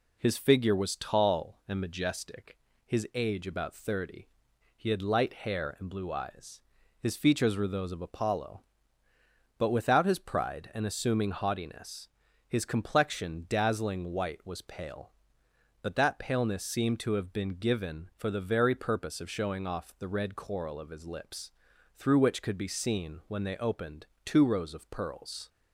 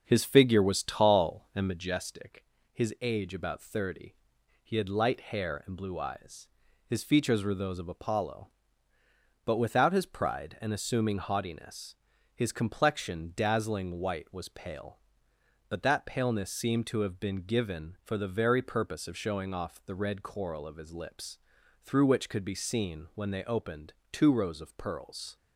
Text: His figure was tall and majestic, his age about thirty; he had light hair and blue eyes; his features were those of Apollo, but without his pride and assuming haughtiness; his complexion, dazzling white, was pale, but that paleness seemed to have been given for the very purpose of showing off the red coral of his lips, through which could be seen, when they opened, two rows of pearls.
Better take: first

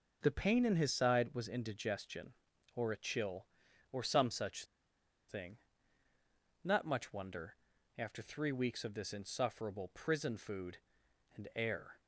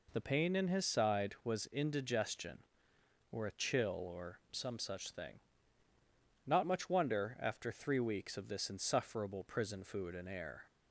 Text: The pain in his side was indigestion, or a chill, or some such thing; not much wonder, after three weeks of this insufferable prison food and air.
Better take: second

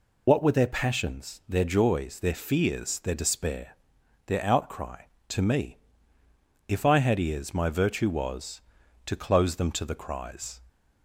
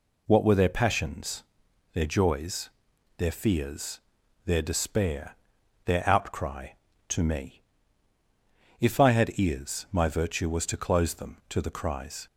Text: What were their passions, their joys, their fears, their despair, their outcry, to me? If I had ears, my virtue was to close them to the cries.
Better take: second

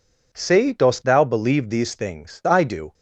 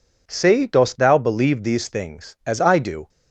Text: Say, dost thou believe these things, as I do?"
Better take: second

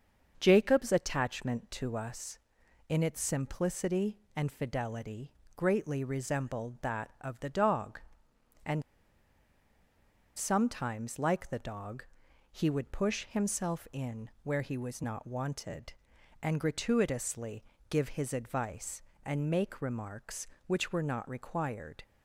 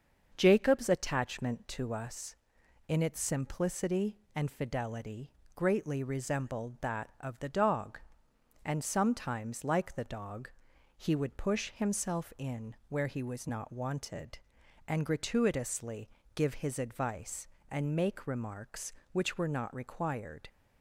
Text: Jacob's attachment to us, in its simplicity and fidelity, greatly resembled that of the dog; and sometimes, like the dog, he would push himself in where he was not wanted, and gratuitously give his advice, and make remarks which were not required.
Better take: second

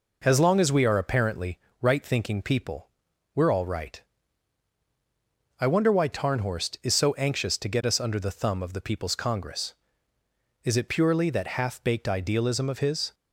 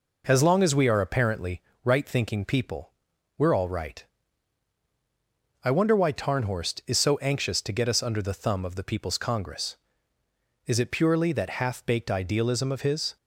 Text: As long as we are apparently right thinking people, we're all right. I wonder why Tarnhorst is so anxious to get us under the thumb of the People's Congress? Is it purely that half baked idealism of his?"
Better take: neither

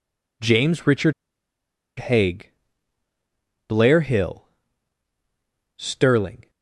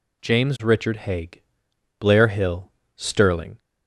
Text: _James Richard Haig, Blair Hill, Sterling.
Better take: second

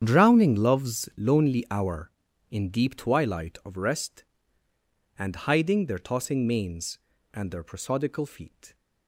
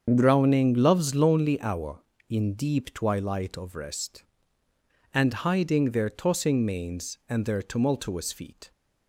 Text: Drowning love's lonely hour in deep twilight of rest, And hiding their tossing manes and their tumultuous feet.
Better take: second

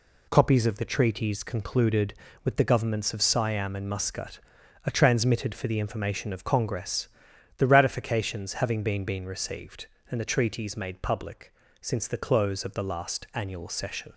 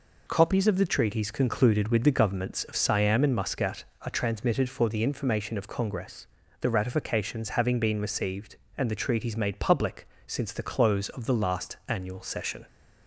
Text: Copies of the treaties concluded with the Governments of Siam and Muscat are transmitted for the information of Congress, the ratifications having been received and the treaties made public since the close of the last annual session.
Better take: second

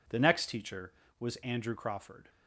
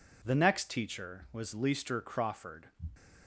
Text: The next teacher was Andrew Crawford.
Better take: first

